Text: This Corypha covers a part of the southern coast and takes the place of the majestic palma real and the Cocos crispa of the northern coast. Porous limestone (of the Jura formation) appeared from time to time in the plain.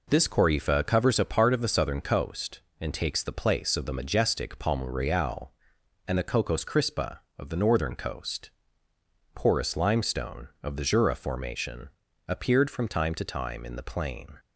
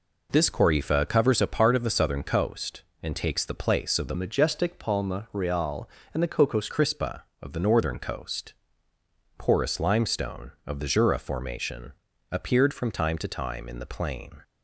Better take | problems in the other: first | changes voice from "majestic" to "Cocos"; from 4.1 to 6.6 s; 2.5 s long

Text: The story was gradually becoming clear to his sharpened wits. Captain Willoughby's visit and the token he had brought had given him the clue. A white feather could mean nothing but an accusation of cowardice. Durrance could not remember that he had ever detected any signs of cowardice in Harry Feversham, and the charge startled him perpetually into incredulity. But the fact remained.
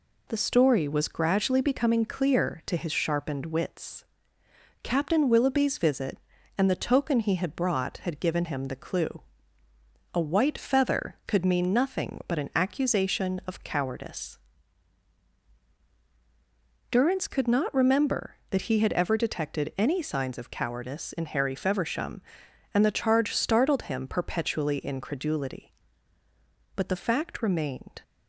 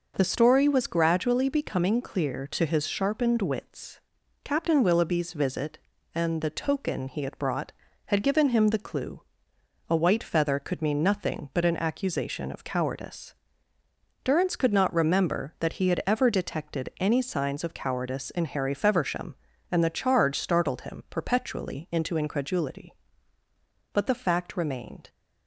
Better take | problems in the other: second | skips "into"; at 24.7 s

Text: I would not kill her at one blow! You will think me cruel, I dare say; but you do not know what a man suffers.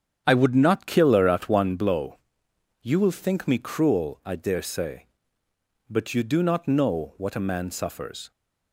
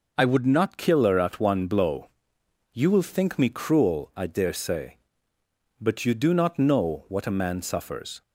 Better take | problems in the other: second | starts louder than the rest; strong; until 1.8 s; 8.5 dB

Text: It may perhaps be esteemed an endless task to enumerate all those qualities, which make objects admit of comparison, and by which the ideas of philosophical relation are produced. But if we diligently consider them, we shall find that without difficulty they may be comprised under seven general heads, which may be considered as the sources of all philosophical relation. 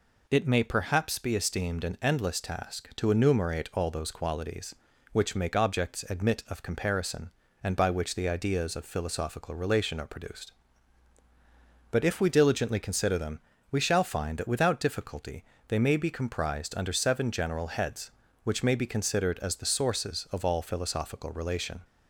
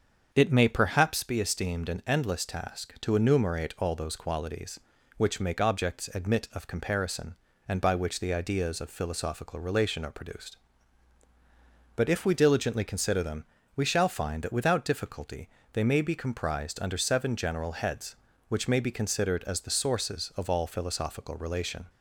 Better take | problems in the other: first | starts louder than the rest; until 1.2 s; 7 dB // pauses between "difficulty" and "they"; slight; at 15.4 s; 0.24 s long; slight in the first

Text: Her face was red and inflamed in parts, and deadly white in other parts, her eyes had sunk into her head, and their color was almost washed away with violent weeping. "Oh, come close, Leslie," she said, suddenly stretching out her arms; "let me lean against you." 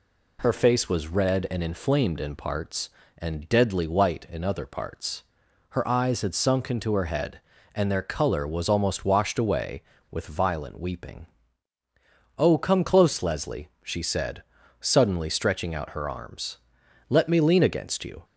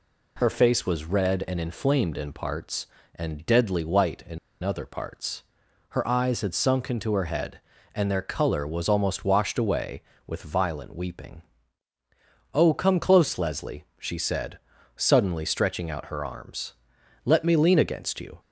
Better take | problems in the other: first | pauses between "in" and "other"; slight; at 4.3 s; 0.23 s long

